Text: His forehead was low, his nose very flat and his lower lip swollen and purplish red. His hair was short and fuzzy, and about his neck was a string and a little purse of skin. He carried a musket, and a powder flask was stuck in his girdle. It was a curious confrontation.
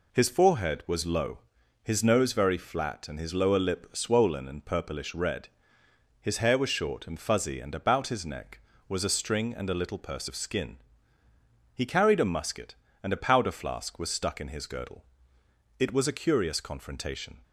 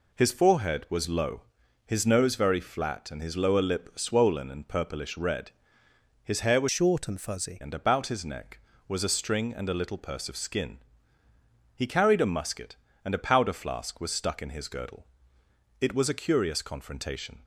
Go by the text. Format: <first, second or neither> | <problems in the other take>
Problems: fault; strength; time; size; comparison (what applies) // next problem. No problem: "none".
first | changes voice from "short" to "fuzzy"; from 6.6 to 7.6 s; 1.0 s long